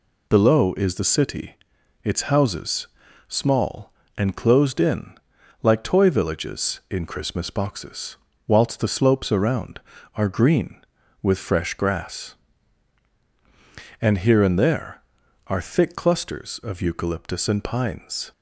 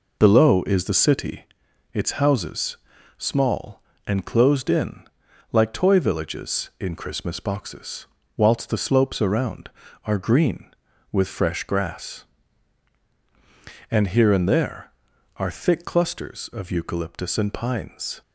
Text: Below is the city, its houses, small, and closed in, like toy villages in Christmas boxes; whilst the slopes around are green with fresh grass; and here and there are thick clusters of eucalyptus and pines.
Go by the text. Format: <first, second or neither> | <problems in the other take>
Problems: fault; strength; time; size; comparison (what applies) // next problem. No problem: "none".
first | starts louder than the rest; noticeable; until 1.6 s; 4.5 dB